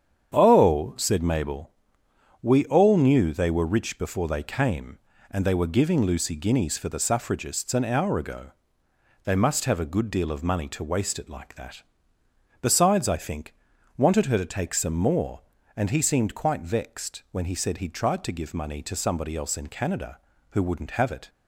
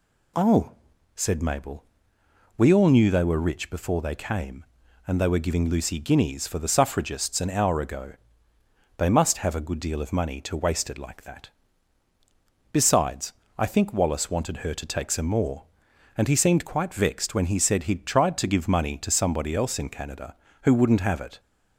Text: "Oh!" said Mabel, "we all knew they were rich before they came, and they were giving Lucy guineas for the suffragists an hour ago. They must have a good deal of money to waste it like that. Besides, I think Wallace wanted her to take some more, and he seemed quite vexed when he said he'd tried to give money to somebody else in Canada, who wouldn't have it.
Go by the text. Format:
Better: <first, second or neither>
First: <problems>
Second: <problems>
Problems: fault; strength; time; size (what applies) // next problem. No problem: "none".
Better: second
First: starts louder than the rest; strong; until 1.3 s; 8.5 dB // skips "Wallace"; at 13.7 s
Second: none